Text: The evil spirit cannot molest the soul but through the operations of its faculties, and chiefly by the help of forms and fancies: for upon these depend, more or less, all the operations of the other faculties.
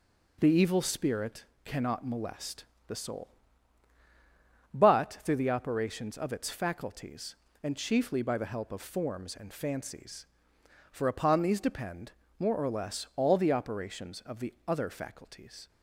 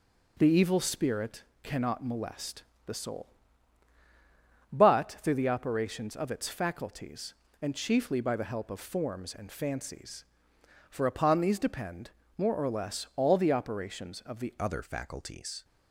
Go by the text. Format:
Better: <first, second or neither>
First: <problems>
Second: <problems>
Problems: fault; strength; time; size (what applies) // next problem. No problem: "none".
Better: first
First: pauses between "spirit" and "cannot"; slight; at 1.4 s; 0.22 s long // pauses between "molest" and "the"; slight; at 2.6 s; 0.24 s long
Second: pauses between "spirit" and "cannot"; slight; at 1.4 s; 0.22 s long // pauses between "molest" and "the"; slight; at 2.6 s; 0.24 s long // changes voice at "other"; from 14.5 s on; 1.1 s long